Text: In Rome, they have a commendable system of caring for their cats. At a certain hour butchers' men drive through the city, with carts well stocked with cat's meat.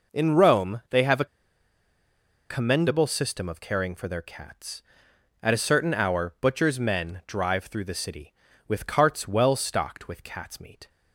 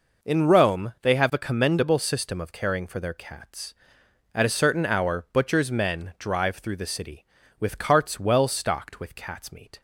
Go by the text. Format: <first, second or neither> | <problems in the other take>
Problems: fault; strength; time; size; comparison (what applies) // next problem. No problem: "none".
second | pauses between "a" and "commendable"; at 1.2 s; 1.2 s long